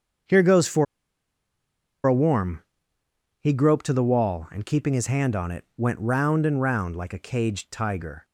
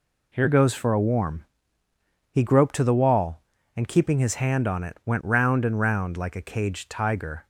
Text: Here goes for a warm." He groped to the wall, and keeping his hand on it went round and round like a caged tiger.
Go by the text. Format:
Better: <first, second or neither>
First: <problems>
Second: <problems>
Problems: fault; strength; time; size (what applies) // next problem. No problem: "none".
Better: second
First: starts louder than the rest; until 2.5 s; 7 dB // pauses between "for" and "a"; at 0.8 s; 1.2 s long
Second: none